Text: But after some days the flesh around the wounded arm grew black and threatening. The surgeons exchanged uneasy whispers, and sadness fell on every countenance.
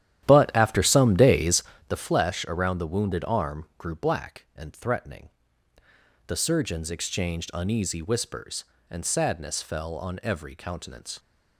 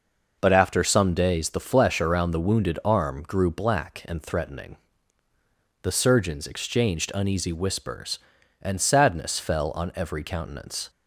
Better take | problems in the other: second | starts louder than the rest; strong; until 2.0 s; 11.5 dB // pauses between "days" and "the"; slight; at 1.6 s; 0.26 s long

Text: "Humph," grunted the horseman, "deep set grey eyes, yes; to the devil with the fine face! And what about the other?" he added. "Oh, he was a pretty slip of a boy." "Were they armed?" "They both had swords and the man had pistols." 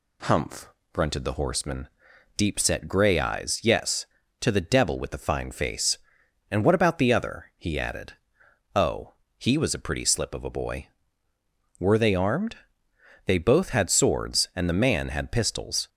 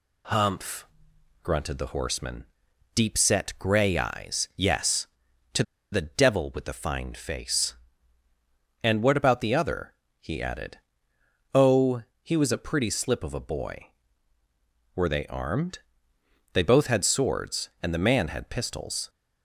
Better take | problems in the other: first | pauses between "to" and "the"; slight; at 5.6 s; 0.30 s long

